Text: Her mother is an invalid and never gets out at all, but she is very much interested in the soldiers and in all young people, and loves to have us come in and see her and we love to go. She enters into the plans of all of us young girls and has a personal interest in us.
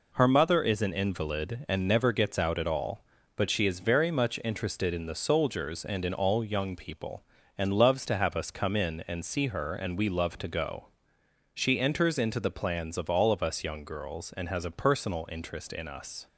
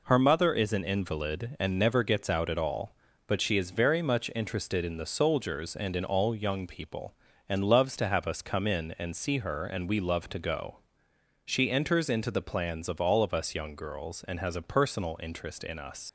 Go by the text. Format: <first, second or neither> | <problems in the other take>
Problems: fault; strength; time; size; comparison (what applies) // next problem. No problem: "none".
first | leaves "us" unfinished; at 16.0 s; 85 ms